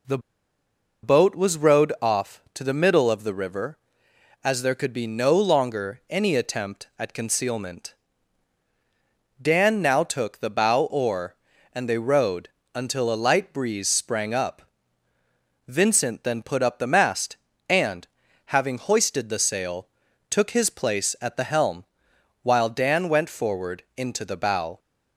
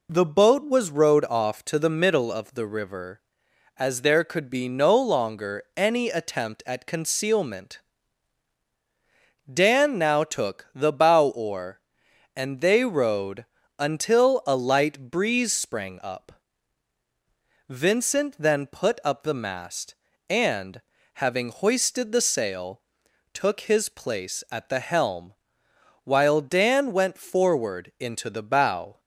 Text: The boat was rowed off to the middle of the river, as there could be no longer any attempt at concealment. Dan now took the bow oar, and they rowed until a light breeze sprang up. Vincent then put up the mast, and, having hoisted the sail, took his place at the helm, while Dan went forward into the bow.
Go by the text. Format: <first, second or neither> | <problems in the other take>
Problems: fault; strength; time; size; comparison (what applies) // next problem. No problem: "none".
second | pauses between "The" and "boat"; noticeable; at 0.1 s; 0.84 s long // pauses between "rowed" and "until"; slight; at 12.4 s; 0.24 s long; slight in the second